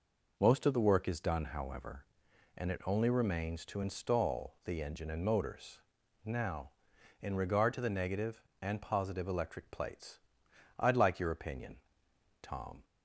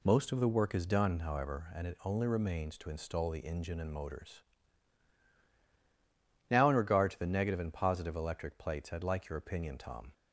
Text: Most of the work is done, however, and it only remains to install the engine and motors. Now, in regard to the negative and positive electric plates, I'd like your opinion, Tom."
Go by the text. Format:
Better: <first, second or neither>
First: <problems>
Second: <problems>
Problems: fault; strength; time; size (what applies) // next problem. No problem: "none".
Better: neither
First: none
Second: none